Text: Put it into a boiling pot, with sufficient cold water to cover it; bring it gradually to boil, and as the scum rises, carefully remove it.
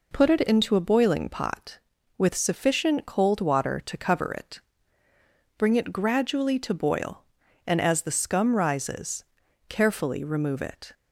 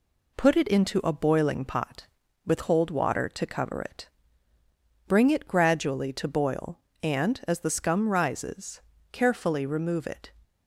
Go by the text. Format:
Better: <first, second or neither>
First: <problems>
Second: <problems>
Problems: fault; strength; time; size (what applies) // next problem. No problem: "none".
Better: first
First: none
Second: skips "sufficient"; at 2.6 s